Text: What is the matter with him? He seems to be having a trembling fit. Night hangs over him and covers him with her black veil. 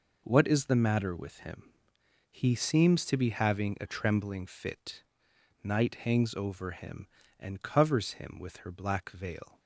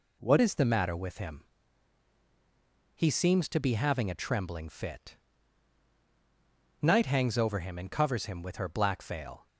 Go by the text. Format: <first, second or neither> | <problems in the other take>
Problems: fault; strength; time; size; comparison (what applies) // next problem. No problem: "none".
first | changes voice at "is"; from 0.3 s on; 9.1 s long